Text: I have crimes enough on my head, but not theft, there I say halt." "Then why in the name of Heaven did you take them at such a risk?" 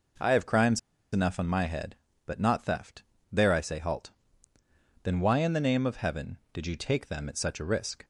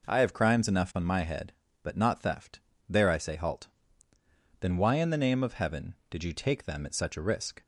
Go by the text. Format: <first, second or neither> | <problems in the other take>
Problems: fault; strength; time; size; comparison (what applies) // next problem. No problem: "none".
second | pauses between "crimes" and "enough"; slight; at 0.7 s; 0.33 s long